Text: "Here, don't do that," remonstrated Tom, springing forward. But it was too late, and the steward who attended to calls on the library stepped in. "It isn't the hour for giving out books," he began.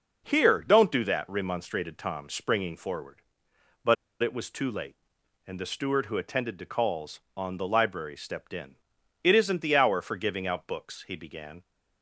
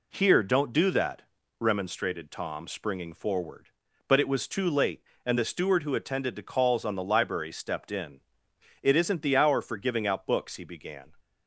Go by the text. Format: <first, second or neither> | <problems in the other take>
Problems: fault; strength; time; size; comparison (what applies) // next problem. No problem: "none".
second | pauses between "But" and "it"; slight; at 3.9 s; 0.27 s long